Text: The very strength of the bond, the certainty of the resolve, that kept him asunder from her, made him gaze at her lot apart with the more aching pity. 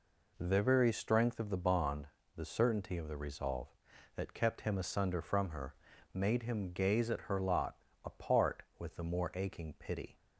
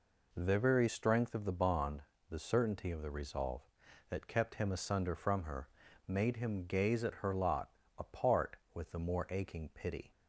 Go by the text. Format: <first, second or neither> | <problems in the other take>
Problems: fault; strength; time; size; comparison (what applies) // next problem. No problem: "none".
neither | pauses between "lot" and "apart"; slight; the same in both